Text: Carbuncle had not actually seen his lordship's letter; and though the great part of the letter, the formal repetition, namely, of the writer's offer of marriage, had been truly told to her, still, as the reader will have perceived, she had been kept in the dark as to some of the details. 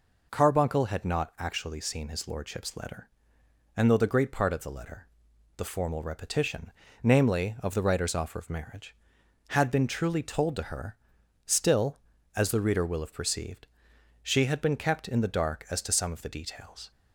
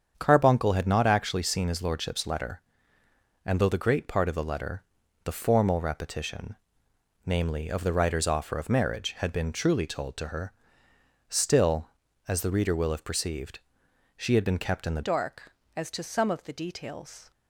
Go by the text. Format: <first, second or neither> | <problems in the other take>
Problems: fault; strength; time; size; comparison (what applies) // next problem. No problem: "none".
first | starts louder than the rest; strong; until 1.1 s; 7.5 dB // changes voice at "dark"; from 15.0 s on; 2.3 s long